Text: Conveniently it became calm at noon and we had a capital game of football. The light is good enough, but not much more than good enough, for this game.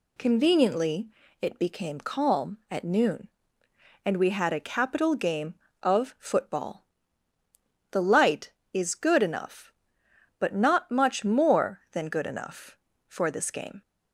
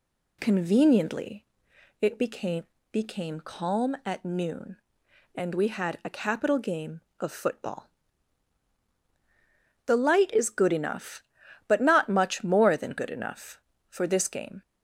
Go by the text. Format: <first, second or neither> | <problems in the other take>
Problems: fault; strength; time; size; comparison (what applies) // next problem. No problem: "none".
first | pauses between "Conveniently" and "it"; noticeable; at 1.4 s; 0.54 s long; slight in the first // says "became" twice; at 2.9 s